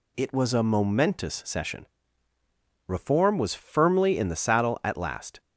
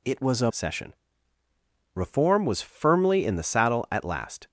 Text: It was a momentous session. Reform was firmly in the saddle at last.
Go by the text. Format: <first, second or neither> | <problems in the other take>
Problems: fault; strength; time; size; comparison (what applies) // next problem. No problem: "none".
first | skips "momentous"; at 0.5 s